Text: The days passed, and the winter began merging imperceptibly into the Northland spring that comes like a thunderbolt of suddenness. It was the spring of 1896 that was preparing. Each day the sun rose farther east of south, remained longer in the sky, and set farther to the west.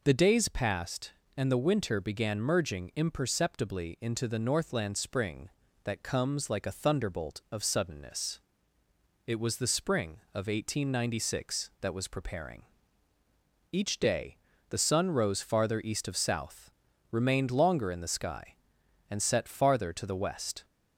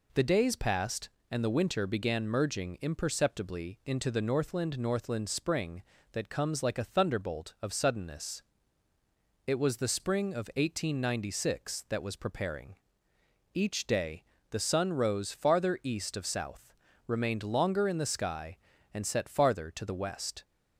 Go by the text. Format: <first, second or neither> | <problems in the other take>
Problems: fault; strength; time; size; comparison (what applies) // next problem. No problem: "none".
first | says "Northland" twice; at 4.7 s // pauses between "day" and "the"; slight; at 14.2 s; 0.26 s long; slight in the first